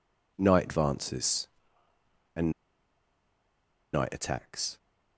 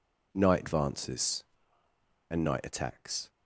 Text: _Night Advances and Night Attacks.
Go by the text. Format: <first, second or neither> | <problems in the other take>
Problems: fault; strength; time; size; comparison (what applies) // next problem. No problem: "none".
second | pauses between "and" and "Night"; strong; at 2.5 s; 1.4 s long